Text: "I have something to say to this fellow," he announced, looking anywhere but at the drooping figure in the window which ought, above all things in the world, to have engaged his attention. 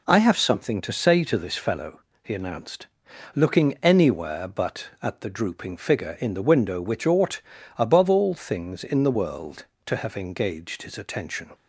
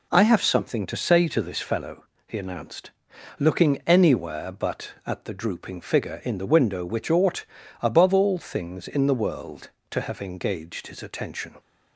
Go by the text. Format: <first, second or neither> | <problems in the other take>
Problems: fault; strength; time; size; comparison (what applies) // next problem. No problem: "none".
neither | none